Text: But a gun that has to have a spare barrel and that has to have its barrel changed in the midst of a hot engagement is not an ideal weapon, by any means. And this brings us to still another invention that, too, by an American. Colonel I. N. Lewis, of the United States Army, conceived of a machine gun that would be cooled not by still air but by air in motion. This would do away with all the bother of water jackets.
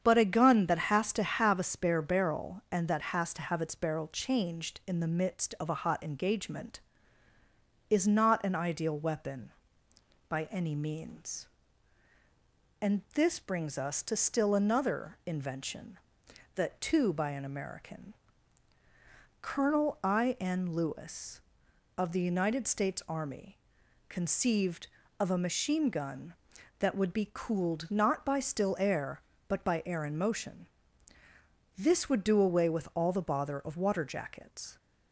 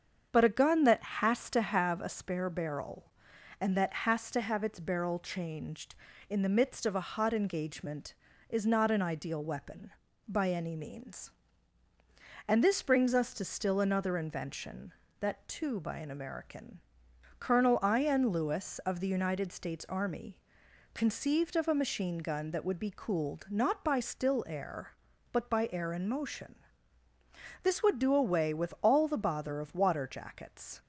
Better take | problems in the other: neither | starts louder than the rest; strong; the same in both

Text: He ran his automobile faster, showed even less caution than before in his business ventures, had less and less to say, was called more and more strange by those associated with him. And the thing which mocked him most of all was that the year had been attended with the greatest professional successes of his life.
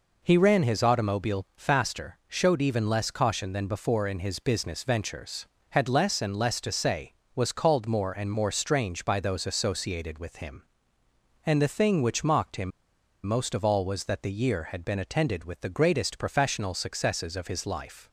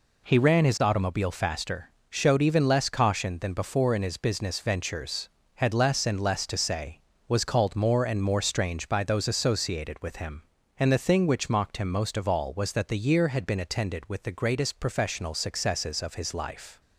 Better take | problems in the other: second | pauses between "him" and "most"; noticeable; at 12.7 s; 0.55 s long

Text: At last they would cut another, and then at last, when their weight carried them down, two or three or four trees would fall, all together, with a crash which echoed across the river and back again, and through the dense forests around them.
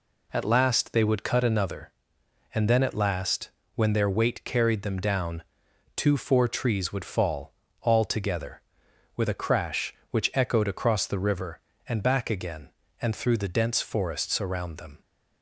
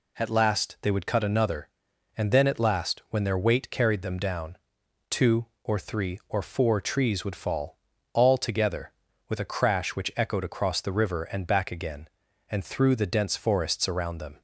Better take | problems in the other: second | skips "or three or"; at 6.1 s

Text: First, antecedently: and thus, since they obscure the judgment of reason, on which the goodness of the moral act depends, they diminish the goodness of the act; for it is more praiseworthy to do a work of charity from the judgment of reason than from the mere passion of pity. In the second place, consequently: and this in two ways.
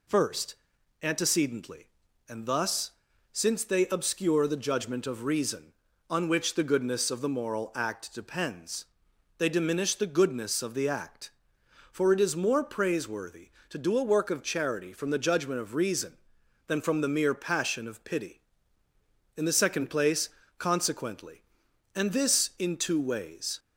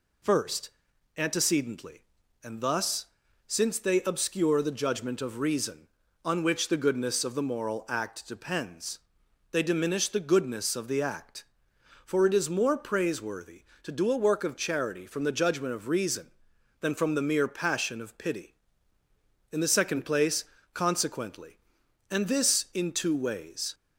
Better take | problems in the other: neither | none

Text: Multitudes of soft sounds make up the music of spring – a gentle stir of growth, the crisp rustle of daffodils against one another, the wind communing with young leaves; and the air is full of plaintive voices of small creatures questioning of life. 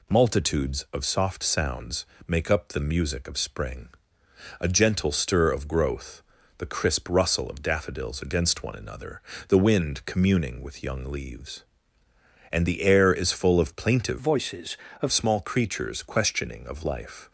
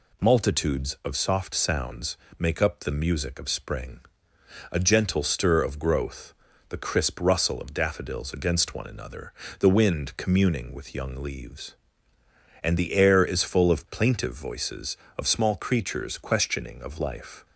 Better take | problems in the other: second | pauses between "sounds" and "make"; slight; at 2.0 s; 0.22 s long; slight in the second // changes voice from "voices" to "of"; from 14.1 to 15.1 s; 1.0 s long

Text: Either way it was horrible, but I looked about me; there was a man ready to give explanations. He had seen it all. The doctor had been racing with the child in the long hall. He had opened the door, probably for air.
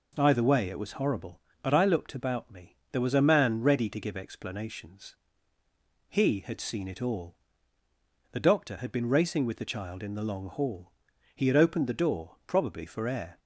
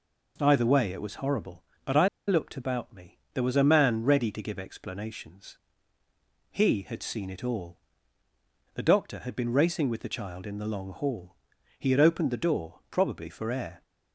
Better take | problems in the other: first | pauses between "I" and "looked"; slight; at 2.0 s; 0.19 s long

